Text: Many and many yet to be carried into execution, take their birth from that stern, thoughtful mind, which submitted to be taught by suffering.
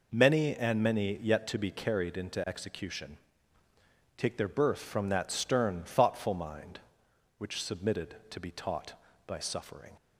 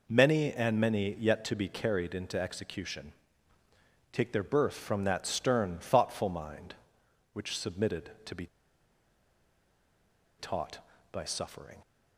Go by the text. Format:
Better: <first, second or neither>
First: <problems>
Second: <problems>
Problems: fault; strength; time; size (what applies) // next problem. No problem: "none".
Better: first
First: none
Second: pauses between "be" and "taught"; strong; at 8.4 s; 1.9 s long